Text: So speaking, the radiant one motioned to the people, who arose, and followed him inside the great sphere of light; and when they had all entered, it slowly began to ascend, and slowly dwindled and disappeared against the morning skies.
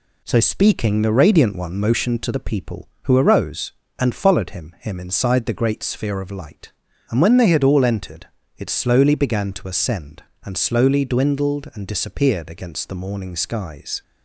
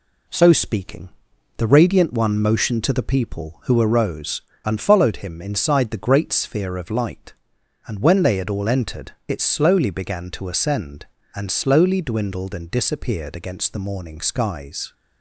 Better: second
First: says "him" twice; at 4.7 s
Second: none

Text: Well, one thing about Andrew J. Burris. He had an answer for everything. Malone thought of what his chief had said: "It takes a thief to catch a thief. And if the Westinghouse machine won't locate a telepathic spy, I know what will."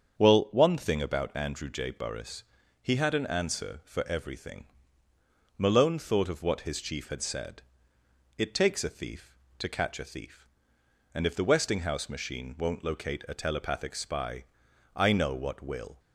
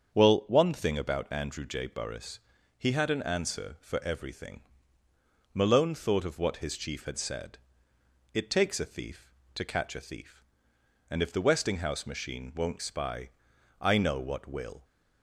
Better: first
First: starts louder than the rest; strong; until 1.2 s; 7.5 dB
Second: starts louder than the rest; strong; until 1.1 s; 7.5 dB // skips "locate a telepathic"; at 12.8 s

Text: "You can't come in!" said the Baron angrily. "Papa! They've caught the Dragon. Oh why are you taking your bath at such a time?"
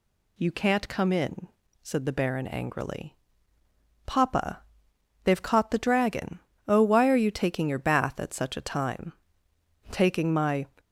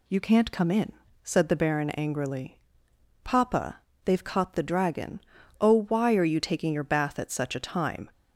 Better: second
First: goes on to say "Taking my"; noticeable; from 9.9 s on; 0.74 s long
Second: none

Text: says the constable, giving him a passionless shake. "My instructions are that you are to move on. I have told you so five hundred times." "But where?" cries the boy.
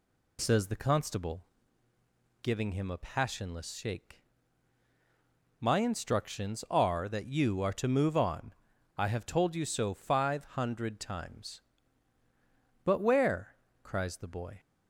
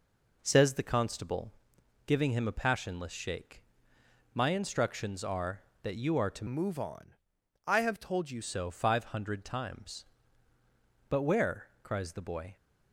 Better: first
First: none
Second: changes voice from "move" to "you"; from 6.4 to 8.4 s; 2.0 s long

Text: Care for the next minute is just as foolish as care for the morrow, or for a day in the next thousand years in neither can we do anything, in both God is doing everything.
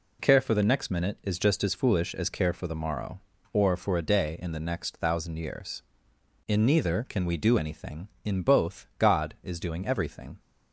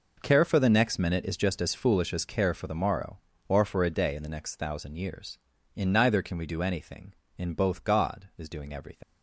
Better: first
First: none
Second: leaves "everything" unfinished; at 9.0 s; 85 ms

